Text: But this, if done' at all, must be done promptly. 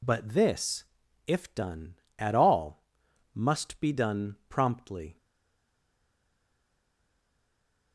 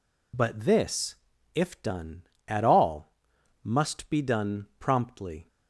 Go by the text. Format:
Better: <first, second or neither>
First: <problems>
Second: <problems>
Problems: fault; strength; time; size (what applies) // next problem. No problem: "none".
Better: second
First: stays silent after the last word; strong; from 5.1 s on; 2.8 s long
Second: none